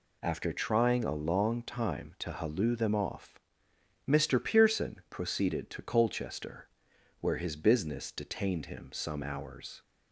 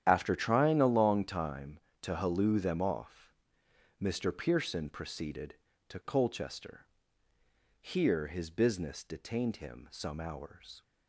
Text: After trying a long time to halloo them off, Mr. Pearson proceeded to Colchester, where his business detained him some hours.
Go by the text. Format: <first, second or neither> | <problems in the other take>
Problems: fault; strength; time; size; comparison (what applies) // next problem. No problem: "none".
first | starts louder than the rest; strong; until 1.0 s; 10 dB // says "here" for "where"; at 7.8 s